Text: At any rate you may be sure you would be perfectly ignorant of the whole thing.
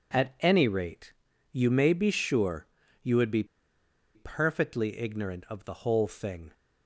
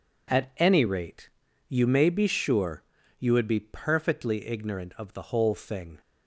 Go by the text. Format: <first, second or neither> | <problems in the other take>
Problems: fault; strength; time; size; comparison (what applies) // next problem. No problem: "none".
second | pauses between "rate" and "you"; at 1.1 s; 0.40 s long; also in the second // pauses between "sure" and "you"; slight; at 2.6 s; 0.36 s long; slight in the second // pauses between "be" and "perfectly"; noticeable; at 3.4 s; 0.70 s long